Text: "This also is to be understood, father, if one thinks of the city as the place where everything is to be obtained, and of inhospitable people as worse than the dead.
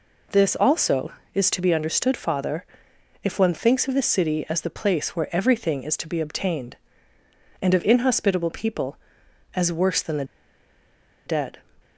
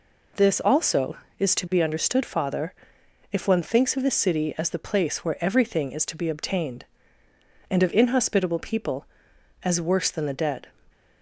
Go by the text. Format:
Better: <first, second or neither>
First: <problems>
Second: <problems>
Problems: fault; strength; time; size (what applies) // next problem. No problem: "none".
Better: second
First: pauses between "the" and "dead"; at 10.2 s; 1.0 s long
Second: none